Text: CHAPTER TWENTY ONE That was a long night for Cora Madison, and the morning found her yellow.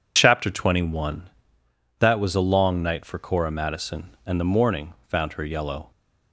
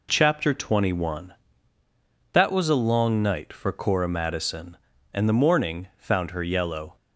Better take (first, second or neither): neither